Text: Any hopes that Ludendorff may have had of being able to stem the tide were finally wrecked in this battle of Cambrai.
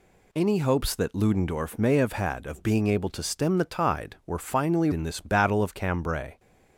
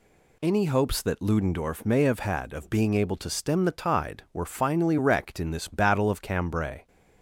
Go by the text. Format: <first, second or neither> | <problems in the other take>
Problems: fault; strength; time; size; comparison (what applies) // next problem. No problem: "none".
second | skips "wrecked"; at 4.9 s